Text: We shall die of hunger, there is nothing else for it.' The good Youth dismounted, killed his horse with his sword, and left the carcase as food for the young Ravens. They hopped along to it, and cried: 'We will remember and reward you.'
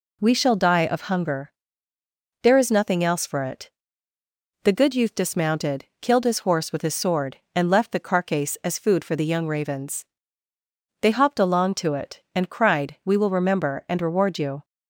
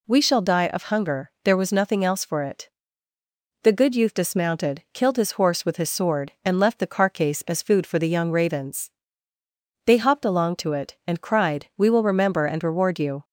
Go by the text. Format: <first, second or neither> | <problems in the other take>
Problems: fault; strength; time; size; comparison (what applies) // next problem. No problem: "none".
first | says "was" for "is"; at 1.5 s